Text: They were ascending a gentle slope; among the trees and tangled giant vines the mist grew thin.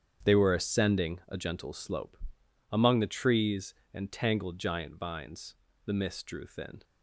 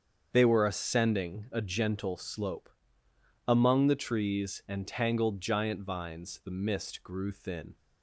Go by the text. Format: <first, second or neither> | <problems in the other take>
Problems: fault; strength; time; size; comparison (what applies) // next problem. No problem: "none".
second | starts louder than the rest; strong; until 1.3 s; 8 dB; strong in the second // pauses between "vines" and "the"; slight; at 5.5 s; 0.30 s long // says "drew" for "grew"; at 6.2 s